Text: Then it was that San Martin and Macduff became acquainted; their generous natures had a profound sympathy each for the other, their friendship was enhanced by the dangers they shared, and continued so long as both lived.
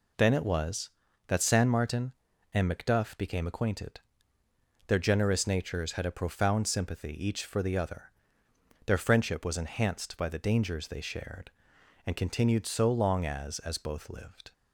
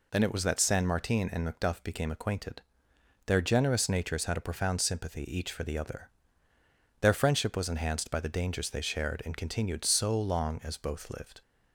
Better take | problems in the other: second | says "as" twice; at 13.6 s

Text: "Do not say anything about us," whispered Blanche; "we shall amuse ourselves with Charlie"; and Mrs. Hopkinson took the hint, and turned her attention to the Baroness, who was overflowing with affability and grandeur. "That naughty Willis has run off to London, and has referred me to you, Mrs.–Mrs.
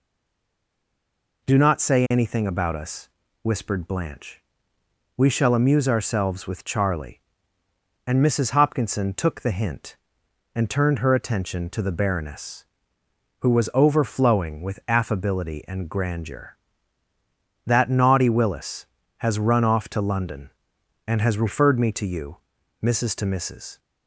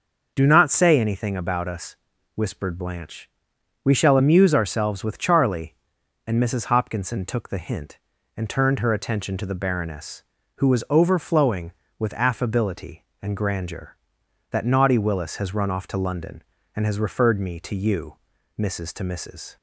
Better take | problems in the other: second | stays silent before the first word; noticeable; until 1.4 s; 1.4 s long

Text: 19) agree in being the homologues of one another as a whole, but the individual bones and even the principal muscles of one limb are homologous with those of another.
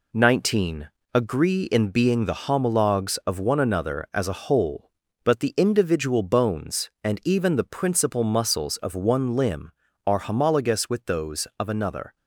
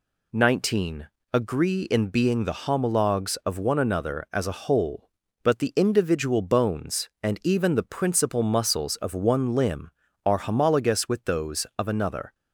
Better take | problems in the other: second | gets quieter; noticeable; throughout; 5 dB

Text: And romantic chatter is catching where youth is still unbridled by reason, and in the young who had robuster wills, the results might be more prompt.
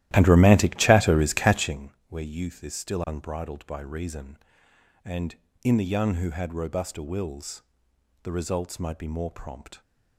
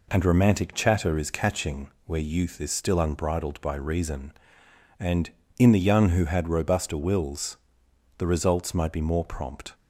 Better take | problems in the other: second | starts louder than the rest; strong; until 1.8 s; 14 dB // pauses between "catching" and "where"; slight; at 1.9 s; 0.18 s long; slight in the second

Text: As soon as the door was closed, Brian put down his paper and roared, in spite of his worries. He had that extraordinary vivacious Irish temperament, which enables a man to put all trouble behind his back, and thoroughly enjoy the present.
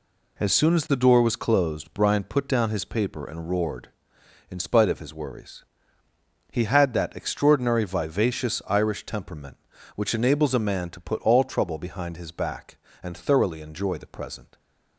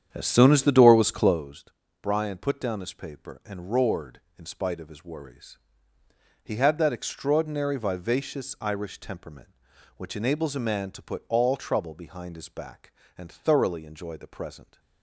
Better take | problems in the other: first | starts louder than the rest; strong; until 1.4 s; 9 dB

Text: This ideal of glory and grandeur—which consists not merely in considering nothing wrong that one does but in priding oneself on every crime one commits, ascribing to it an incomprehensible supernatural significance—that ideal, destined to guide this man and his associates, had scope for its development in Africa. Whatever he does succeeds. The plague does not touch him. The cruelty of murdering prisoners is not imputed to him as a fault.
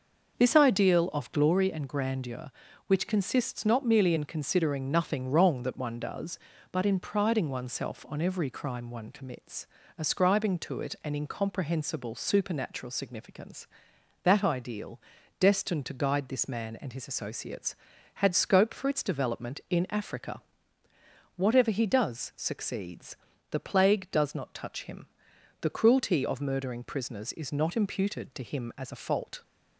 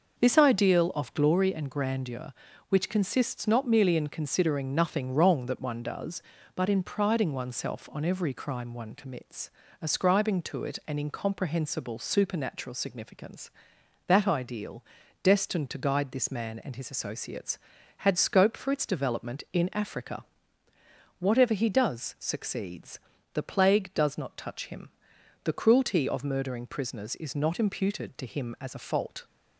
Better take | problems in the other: neither | starts louder than the rest; noticeable; the same in both

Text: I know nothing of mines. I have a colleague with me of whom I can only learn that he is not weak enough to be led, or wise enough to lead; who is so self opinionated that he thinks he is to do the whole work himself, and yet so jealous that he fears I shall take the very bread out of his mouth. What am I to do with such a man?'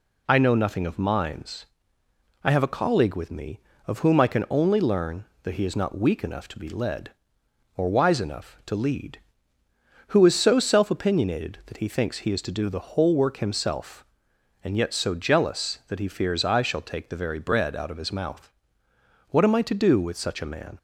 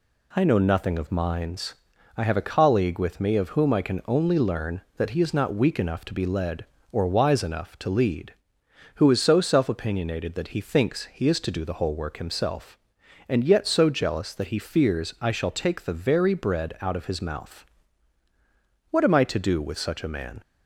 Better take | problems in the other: neither | none

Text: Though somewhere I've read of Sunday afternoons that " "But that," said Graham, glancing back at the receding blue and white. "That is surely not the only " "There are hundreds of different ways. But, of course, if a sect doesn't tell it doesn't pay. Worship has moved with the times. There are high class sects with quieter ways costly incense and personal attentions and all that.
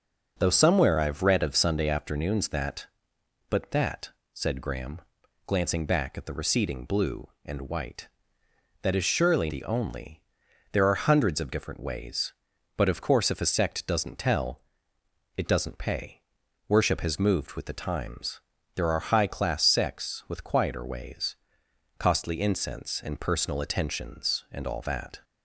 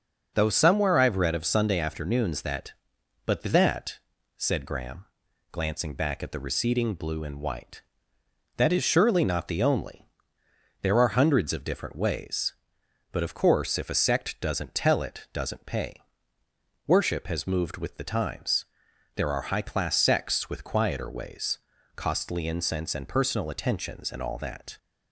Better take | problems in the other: second | starts louder than the rest; strong; until 1.4 s; 7 dB; also in the second // skips "not"; at 9.4 s // pauses between "tell" and "it"; noticeable; at 14.6 s; 0.74 s long // pauses between "ways" and "costly"; noticeable; at 21.3 s; 0.62 s long; also in the second

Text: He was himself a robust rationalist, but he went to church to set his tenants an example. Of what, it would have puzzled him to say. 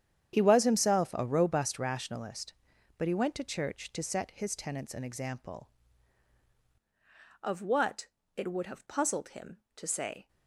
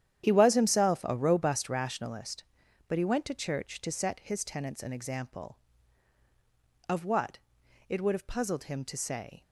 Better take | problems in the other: second | starts louder than the rest; strong; until 1.3 s; 9 dB; strong in the second // changes voice at "Of"; from 7.4 s on; 2.8 s long

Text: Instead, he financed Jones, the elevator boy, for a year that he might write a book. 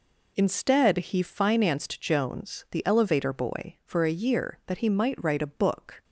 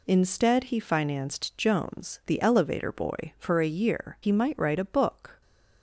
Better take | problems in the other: first | skips "that"; at 4.1 s

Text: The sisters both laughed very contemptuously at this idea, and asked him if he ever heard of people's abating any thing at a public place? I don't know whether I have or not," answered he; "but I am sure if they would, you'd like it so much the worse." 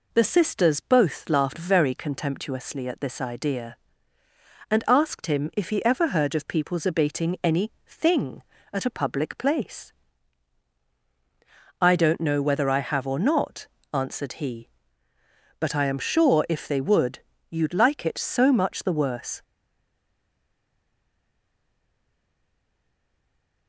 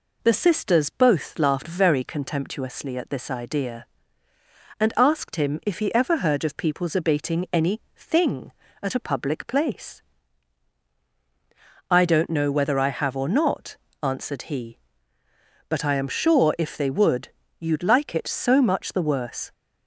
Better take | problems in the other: second | pauses between "any" and "thing"; slight; at 7.7 s; 0.16 s long; slight in the second // stays silent after the last word; strong; from 19.4 s on; 4.2 s long

